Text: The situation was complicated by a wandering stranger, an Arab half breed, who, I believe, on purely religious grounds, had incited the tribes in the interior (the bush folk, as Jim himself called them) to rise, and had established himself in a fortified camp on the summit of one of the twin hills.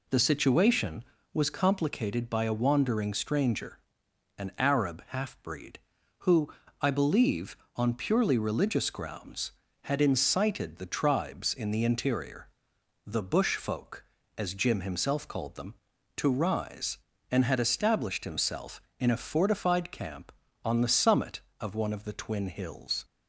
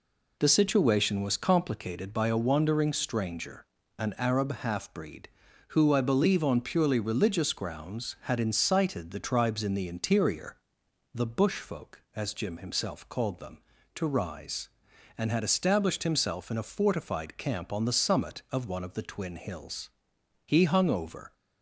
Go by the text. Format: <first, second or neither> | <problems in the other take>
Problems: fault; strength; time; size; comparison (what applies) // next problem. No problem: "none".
first | goes on to say "He hung over"; noticeable; from 20.4 s on; 0.88 s long